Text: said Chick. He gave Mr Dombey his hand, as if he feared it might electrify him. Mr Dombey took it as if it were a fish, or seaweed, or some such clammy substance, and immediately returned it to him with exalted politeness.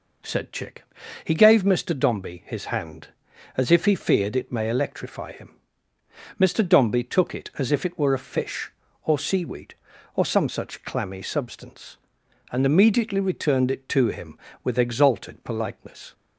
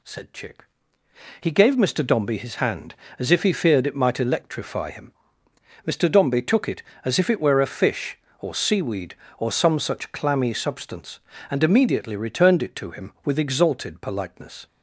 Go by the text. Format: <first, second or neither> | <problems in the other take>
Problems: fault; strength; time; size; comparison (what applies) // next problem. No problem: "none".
second | says "may" for "might"; at 4.5 s